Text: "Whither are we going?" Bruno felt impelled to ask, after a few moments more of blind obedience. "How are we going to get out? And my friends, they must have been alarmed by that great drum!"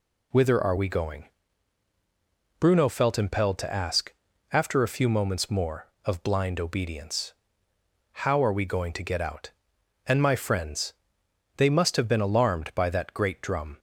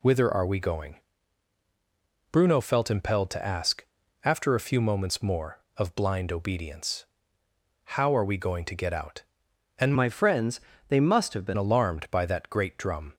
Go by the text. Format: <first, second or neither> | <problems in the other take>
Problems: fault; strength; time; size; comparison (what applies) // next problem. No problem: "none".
first | changes voice from "my" to "been"; from 9.9 to 11.5 s; 1.6 s long